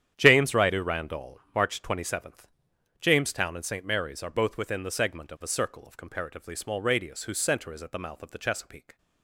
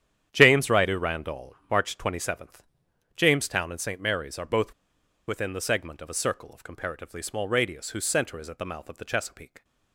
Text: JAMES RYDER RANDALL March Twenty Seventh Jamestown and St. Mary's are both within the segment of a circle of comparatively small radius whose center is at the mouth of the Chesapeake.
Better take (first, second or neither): first